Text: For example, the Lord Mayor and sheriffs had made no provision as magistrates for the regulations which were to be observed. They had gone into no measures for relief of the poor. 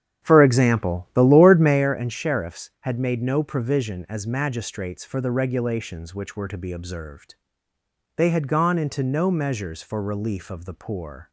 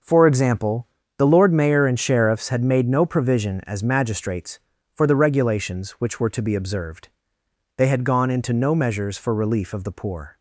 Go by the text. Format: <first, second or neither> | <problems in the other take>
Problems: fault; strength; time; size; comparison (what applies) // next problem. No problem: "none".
second | starts louder than the rest; strong; until 1.9 s; 9 dB